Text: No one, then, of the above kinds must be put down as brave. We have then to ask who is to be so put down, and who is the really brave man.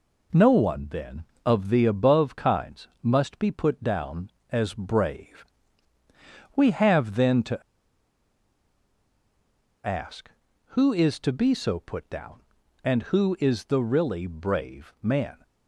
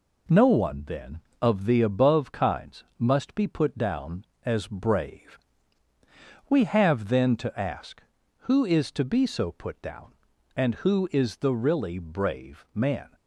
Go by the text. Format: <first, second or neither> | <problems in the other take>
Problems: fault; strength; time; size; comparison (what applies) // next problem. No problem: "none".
second | pauses between "kinds" and "must"; slight; at 2.8 s; 0.16 s long; slight in the second // pauses between "to" and "ask"; strong; at 7.6 s; 2.2 s long